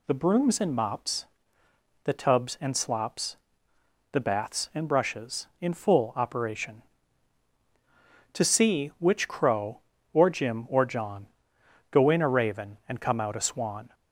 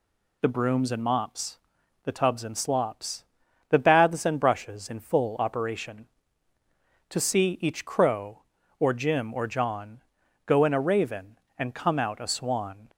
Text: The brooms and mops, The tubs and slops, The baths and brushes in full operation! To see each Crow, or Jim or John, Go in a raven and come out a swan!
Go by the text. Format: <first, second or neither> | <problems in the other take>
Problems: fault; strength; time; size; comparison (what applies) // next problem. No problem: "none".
second | says "which" for "each"; at 8.9 s